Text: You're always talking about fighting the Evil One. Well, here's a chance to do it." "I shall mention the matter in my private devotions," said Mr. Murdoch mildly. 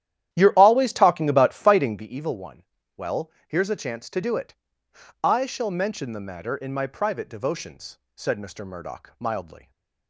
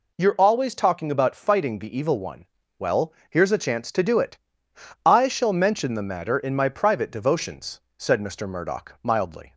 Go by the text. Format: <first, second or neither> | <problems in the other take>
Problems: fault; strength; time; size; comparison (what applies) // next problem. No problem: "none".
second | starts louder than the rest; strong; until 2.1 s; 11.5 dB // stays silent after the last word; slight; from 9.5 s on; 0.5 s long